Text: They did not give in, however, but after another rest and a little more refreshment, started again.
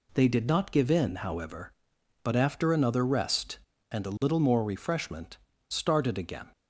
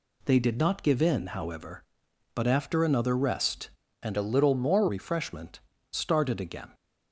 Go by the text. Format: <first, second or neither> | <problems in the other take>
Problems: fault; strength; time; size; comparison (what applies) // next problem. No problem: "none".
first | changes voice from "a" to "more"; from 4.1 to 4.8 s; 0.7 s long